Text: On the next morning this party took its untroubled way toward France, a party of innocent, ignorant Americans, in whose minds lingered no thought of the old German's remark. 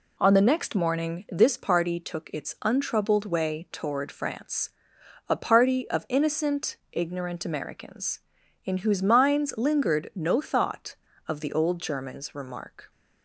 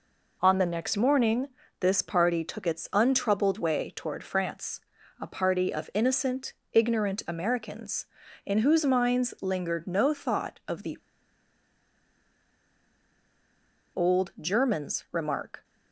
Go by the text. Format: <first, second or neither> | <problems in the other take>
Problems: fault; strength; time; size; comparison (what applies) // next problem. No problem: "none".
first | pauses between "morning" and "this"; slight; at 1.4 s; 0.32 s long // pauses between "the" and "old"; strong; at 10.9 s; 2.9 s long